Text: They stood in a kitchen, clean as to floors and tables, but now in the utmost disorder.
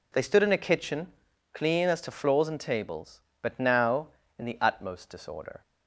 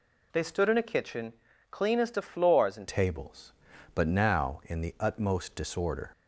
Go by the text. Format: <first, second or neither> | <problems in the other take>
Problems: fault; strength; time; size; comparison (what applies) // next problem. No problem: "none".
first | changes voice at "tables"; from 2.8 s on; 3.3 s long